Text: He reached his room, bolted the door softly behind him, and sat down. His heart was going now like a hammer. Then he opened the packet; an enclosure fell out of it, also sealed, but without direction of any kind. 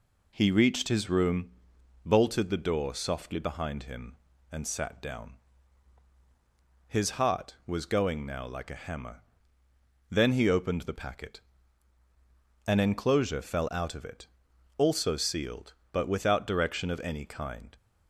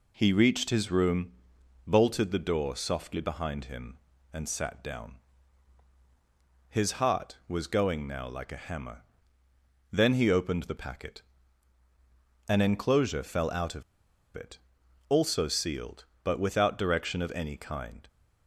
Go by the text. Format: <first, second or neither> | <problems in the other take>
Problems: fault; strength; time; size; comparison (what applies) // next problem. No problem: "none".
first | pauses between "of" and "it"; noticeable; at 13.8 s; 0.52 s long